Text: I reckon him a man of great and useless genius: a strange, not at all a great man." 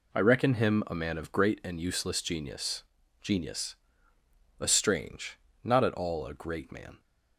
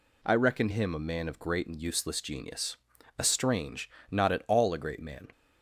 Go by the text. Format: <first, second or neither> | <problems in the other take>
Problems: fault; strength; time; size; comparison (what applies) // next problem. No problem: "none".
second | says "genius" twice; at 3.2 s